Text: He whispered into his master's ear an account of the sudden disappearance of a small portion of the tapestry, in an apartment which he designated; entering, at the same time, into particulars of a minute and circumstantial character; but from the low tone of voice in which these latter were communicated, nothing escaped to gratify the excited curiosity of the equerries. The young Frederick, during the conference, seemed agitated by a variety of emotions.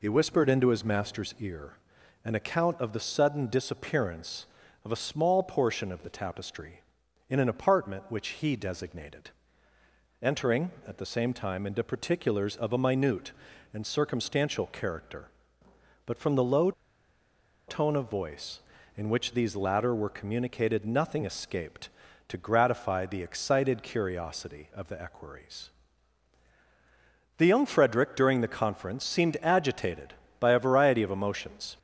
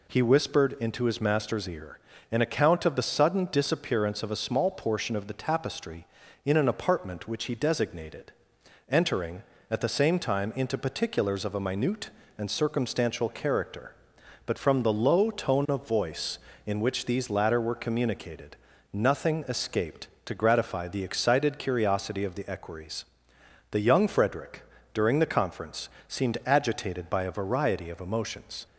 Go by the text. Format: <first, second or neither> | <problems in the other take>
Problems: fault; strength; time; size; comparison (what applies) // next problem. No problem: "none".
second | pauses between "ear" and "an"; noticeable; at 1.7 s; 0.48 s long; slight in the second // pauses between "low" and "tone"; noticeable; at 16.7 s; 0.95 s long